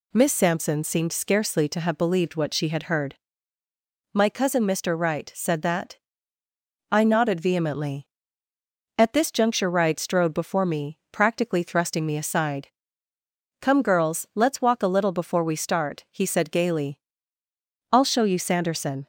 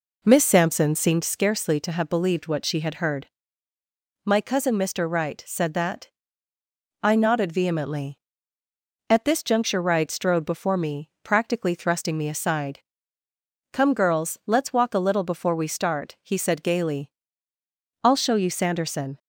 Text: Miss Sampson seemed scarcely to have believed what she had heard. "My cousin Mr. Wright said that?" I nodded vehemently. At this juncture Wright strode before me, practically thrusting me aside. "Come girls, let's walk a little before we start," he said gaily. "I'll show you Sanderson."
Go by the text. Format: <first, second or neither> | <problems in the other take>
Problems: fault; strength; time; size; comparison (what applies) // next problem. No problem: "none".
first | starts louder than the rest; noticeable; until 1.4 s; 4 dB